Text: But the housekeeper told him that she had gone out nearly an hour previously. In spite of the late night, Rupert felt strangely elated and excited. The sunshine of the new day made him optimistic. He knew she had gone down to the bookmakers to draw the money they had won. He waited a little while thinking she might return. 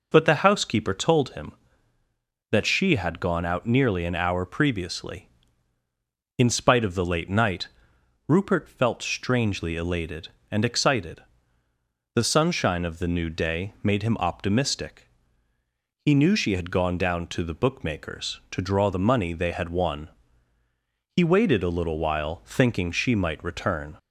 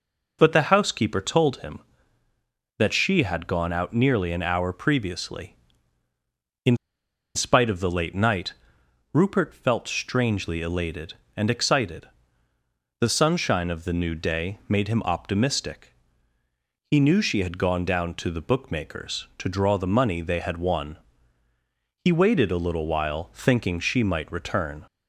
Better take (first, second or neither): first